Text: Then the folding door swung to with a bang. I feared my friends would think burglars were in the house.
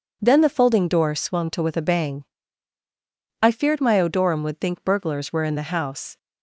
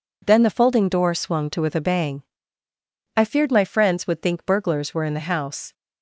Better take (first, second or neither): second